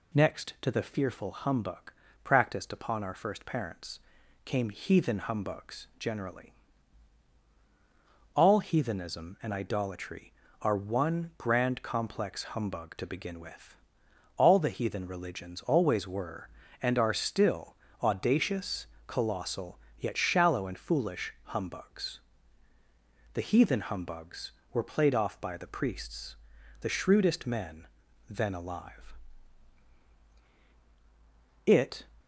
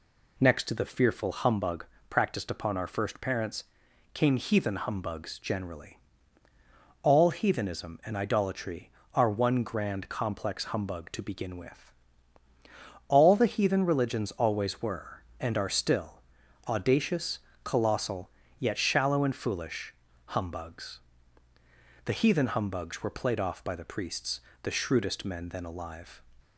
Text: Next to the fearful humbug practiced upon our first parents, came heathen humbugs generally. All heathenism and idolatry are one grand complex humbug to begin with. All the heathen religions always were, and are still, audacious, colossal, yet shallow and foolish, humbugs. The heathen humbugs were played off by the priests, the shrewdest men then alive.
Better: second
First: pauses between "humbug" and "practiced"; slight; at 1.9 s; 0.32 s long // pauses between "men" and "then"; at 27.8 s; 0.40 s long // goes on to say "It"; slight; from 31.6 s on; 0.38 s long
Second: pauses between "humbug" and "practiced"; slight; at 1.8 s; 0.24 s long

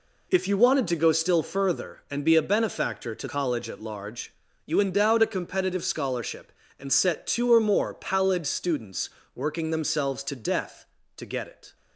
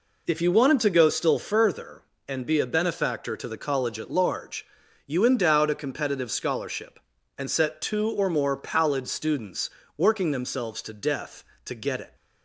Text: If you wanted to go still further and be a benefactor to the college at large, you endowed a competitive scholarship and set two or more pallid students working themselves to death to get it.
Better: second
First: skips "the"; at 3.2 s // pauses between "students" and "working"; slight; at 9.0 s; 0.26 s long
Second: pauses between "students" and "working"; slight; at 9.6 s; 0.30 s long

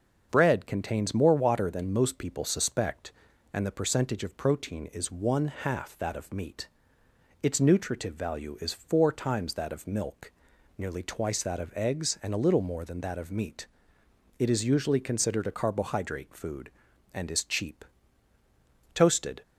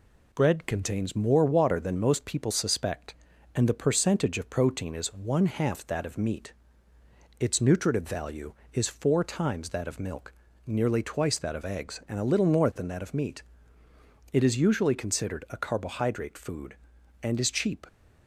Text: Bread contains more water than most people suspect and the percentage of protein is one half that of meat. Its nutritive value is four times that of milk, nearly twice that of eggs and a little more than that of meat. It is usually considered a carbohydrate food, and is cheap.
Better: second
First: starts louder than the rest; until 1.3 s; 7 dB // goes on to say "Toasted"; from 18.9 s on; 0.50 s long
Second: none

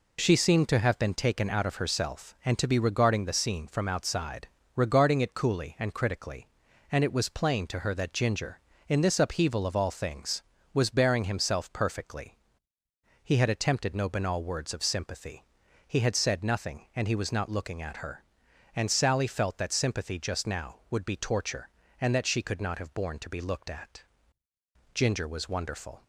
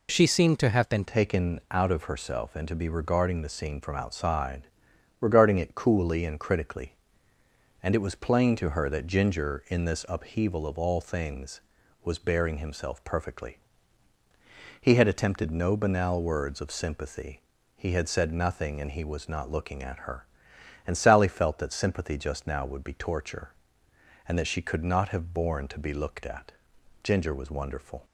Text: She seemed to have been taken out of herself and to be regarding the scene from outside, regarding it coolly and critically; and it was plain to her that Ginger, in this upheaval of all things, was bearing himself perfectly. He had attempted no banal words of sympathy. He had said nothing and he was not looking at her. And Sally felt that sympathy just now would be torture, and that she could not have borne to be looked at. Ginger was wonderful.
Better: first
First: none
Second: changes voice at "taken"; from 1.0 s on; 27.0 s long

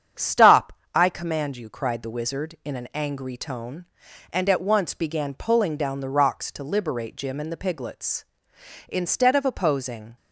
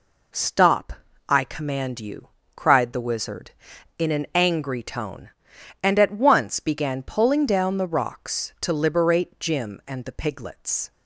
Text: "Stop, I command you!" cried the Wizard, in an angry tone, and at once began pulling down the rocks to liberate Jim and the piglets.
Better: second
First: starts louder than the rest; strong; until 1.4 s; 8.5 dB // goes on to say "Instead of opposing"; noticeable; from 8.8 s on; 1.2 s long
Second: none

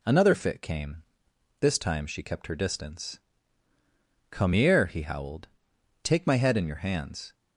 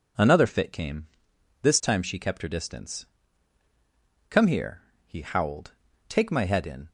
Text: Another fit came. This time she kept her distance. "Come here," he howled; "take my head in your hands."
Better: first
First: none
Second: stops before "your hands"; at 6.8 s

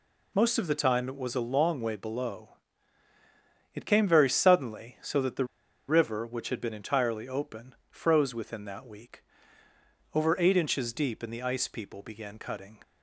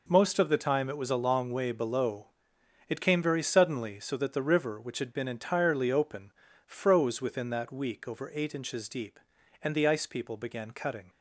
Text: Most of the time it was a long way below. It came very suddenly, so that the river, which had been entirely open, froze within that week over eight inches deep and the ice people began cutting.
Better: second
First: pauses between "the" and "river"; at 5.4 s; 0.43 s long // pauses between "week" and "over"; noticeable; at 9.2 s; 0.90 s long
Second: none

